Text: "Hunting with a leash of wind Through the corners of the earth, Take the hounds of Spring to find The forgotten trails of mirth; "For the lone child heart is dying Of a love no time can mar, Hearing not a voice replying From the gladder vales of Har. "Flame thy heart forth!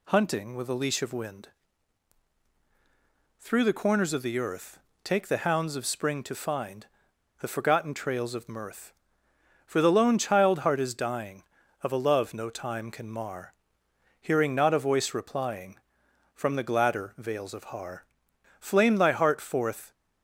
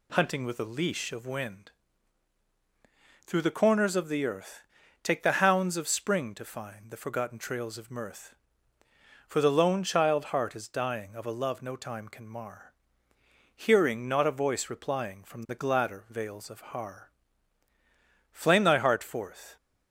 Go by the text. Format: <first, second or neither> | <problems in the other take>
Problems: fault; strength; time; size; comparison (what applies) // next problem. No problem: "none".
second | pauses between "wind" and "Through"; strong; at 1.4 s; 1.9 s long; strong in the second // pauses between "find" and "The"; noticeable; at 6.8 s; 0.55 s long